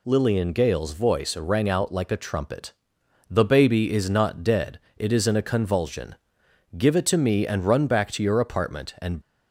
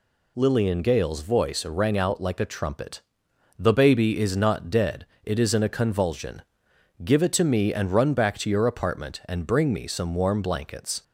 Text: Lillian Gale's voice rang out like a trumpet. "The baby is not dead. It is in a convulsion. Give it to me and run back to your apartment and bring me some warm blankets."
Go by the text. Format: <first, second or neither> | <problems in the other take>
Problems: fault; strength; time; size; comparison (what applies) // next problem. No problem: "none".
second | stops before "bring me some warm blankets"; at 9.2 s